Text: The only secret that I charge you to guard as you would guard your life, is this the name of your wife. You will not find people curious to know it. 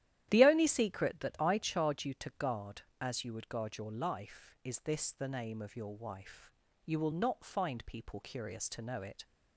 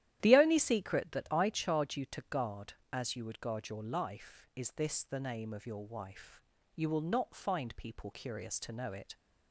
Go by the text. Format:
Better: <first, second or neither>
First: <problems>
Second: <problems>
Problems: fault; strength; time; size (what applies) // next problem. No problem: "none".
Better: neither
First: starts louder than the rest; strong; until 1.3 s; 12 dB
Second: starts louder than the rest; strong; until 1.2 s; 12 dB